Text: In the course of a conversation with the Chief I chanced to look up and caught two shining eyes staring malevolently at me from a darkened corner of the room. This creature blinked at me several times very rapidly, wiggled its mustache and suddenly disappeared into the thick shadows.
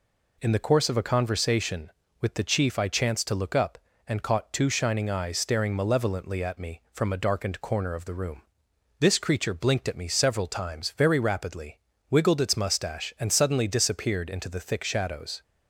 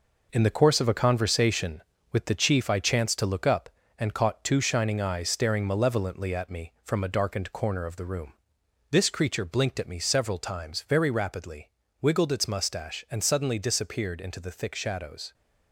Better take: first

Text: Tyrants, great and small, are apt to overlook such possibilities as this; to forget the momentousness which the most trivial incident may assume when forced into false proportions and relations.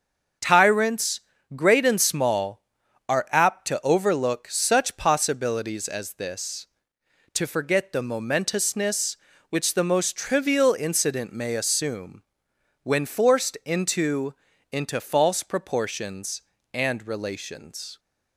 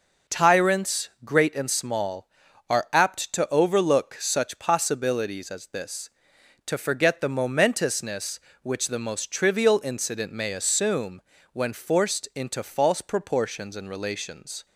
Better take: second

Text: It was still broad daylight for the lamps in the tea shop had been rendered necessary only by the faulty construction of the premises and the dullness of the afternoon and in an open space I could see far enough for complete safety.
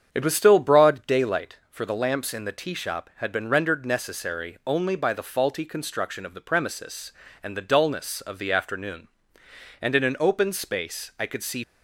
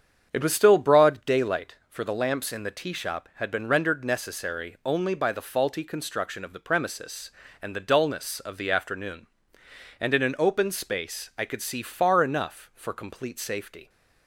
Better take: second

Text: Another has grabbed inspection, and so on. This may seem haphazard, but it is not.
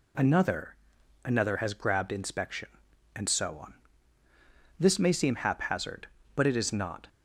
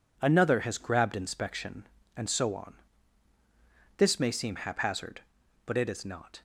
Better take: second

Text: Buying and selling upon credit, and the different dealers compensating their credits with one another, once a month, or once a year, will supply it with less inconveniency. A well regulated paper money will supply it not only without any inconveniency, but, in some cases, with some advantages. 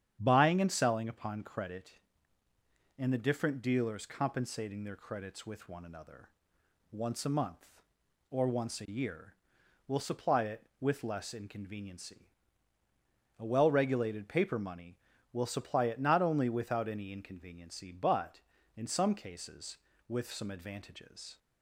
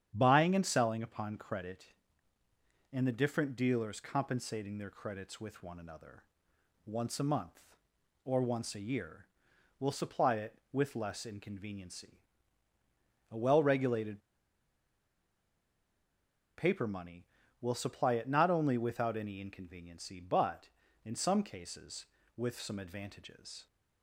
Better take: first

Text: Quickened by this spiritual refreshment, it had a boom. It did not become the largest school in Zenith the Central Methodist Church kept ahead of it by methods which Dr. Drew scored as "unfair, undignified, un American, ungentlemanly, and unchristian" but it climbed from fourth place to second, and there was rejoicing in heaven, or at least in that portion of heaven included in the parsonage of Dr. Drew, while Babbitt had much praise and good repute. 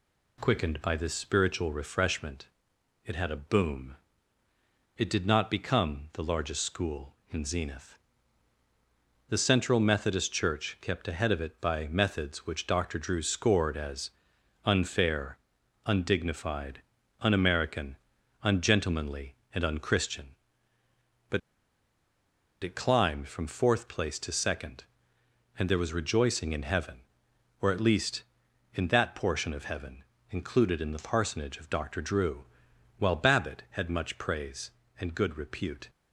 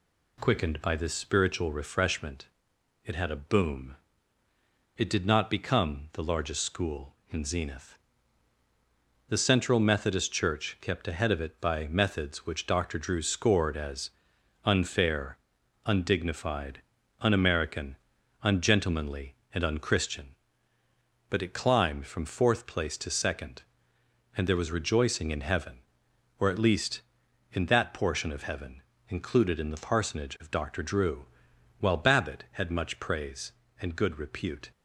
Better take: second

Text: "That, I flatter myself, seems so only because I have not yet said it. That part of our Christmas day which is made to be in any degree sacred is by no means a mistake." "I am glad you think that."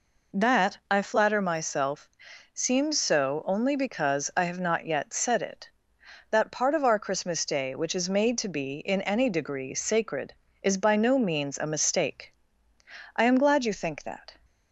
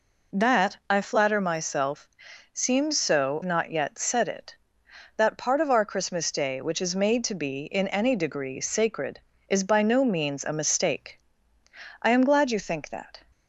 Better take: first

